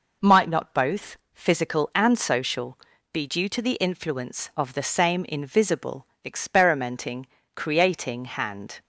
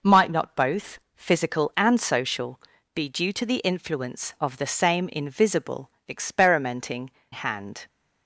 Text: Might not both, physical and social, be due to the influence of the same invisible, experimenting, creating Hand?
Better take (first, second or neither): first